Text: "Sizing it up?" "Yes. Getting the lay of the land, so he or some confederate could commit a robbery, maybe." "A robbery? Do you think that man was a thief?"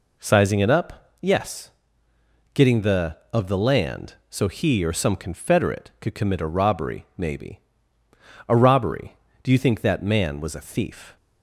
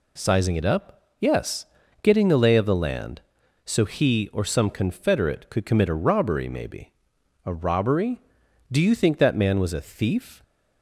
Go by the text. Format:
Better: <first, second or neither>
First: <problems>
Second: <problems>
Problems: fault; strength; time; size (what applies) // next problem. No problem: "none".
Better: second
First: skips "lay"; at 3.2 s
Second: none